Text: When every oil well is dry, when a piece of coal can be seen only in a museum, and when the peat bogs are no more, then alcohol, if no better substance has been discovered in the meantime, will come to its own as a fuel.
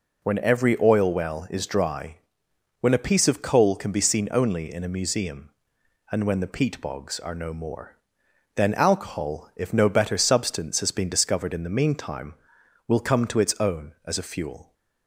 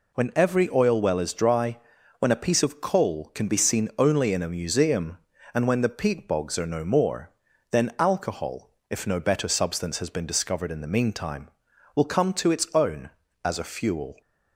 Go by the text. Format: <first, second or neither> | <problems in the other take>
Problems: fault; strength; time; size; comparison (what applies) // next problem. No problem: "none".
neither | none